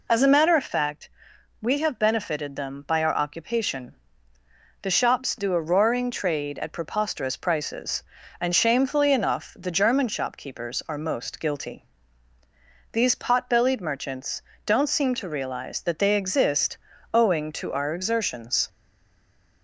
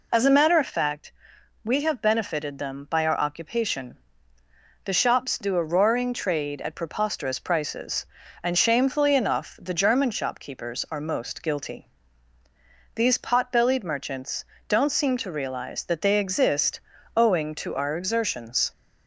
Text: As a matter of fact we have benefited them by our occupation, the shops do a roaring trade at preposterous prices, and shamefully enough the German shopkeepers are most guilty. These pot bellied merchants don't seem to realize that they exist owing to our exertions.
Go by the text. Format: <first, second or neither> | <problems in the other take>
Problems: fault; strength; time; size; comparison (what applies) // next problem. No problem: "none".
second | pauses between "fact" and "we"; noticeable; at 1.0 s; 0.54 s long; noticeable in the second // pauses between "merchants" and "don't"; slight; at 14.4 s; 0.24 s long; slight in the second // pauses between "exist" and "owing"; at 16.7 s; 0.38 s long; also in the second // stays silent after the last word; slight; from 18.6 s on; 1.0 s long